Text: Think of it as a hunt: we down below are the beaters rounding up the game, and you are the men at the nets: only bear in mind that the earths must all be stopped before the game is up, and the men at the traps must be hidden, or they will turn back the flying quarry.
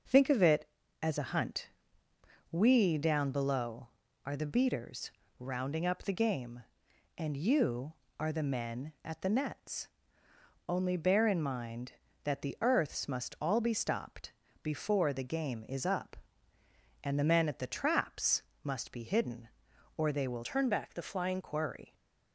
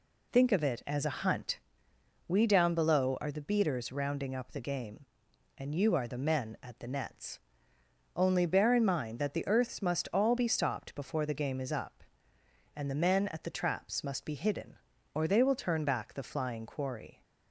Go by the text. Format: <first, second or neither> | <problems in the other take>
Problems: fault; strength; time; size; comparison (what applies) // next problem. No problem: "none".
second | starts louder than the rest; until 1.4 s; 6 dB // pauses between "beaters" and "rounding"; slight; at 5.1 s; 0.30 s long // pauses between "stopped" and "before"; slight; at 14.3 s; 0.32 s long // pauses between "traps" and "must"; slight; at 18.4 s; 0.20 s long // changes voice from "turn" to "flying"; from 20.4 to 21.4 s; 1.0 s long